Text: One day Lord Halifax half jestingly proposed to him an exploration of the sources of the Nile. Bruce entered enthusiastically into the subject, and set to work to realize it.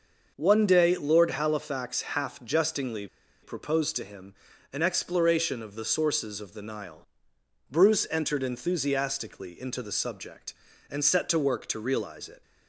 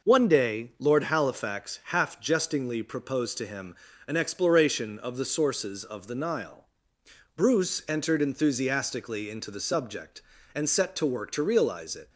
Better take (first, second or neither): second